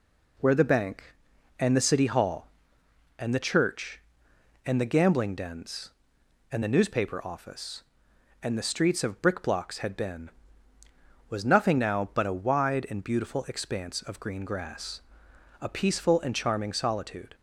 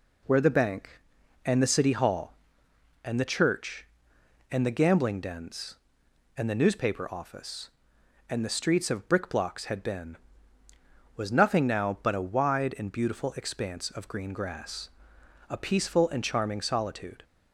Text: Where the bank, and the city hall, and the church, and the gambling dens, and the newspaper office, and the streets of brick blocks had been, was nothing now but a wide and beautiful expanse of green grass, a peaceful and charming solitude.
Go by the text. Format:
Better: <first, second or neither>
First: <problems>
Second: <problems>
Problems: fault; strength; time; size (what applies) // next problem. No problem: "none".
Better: neither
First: none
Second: none